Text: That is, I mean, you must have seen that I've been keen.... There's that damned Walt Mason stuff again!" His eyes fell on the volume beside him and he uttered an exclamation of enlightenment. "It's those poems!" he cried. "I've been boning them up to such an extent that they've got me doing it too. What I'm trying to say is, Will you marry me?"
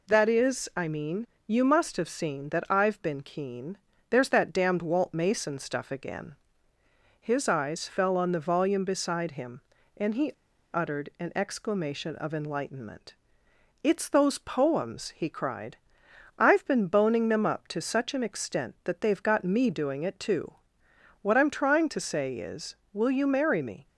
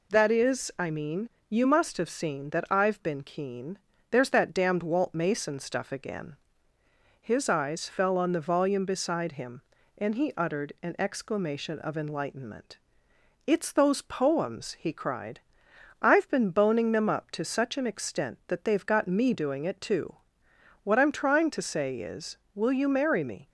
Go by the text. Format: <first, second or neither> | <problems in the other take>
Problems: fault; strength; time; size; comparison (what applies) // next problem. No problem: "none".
second | pauses between "he" and "uttered"; at 10.2 s; 0.43 s long